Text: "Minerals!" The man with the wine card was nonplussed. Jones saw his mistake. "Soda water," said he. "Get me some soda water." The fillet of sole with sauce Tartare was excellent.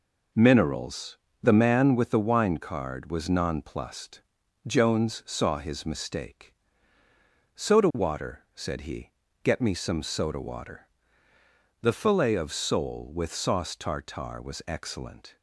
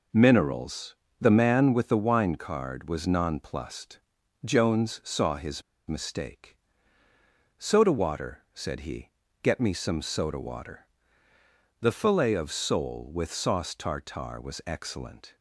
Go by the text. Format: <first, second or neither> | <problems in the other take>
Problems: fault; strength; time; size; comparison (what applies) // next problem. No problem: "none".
first | pauses between "his" and "mistake"; slight; at 5.6 s; 0.25 s long